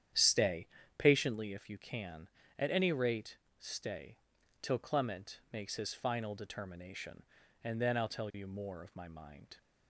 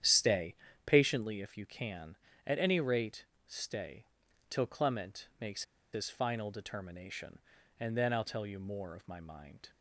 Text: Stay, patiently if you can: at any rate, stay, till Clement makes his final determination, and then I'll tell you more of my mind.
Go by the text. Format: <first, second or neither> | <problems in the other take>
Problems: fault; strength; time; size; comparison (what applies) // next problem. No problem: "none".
first | starts louder than the rest; strong; until 1.3 s; 9.5 dB; strong in the first // pauses between "makes" and "his"; slight; at 5.6 s; 0.31 s long